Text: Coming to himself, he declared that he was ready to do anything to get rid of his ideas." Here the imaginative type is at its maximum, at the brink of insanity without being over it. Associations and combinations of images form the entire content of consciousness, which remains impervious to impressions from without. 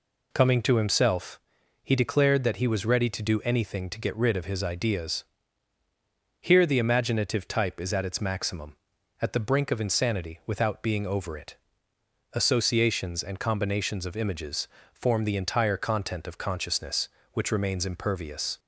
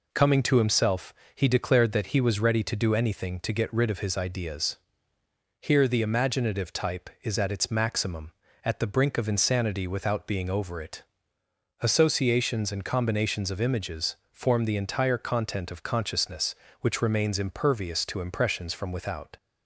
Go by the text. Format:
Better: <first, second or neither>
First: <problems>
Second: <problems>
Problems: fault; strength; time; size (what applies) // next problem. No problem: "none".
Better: second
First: pauses between "images" and "form"; slight; at 14.6 s; 0.26 s long // stops before "to impressions from without"; at 18.5 s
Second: pauses between "images" and "form"; slight; at 14.1 s; 0.16 s long